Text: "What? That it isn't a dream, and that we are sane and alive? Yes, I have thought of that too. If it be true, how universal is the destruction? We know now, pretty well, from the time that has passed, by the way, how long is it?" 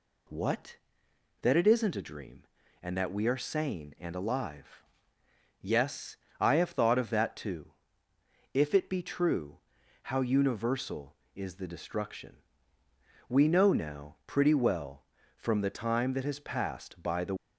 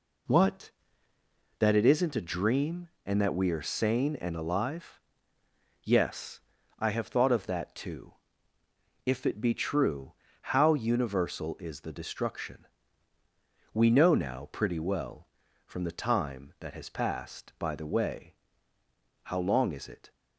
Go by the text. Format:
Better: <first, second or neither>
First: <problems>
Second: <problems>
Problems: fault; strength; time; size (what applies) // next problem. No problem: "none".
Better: second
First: stops before "way how long is it"; at 17.3 s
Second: none